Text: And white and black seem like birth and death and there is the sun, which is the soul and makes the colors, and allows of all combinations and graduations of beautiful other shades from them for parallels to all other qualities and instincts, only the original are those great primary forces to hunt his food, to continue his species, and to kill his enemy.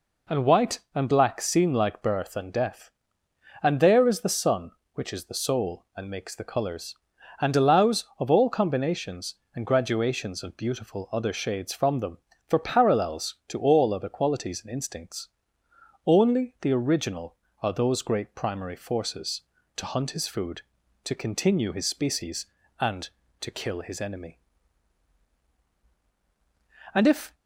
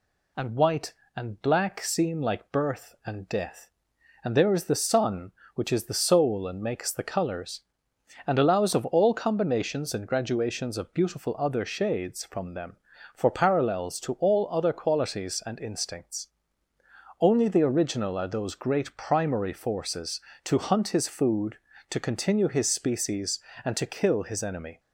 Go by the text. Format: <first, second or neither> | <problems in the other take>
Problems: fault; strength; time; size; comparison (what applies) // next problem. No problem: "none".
second | goes on to say "And if"; slight; from 26.9 s on; 0.40 s long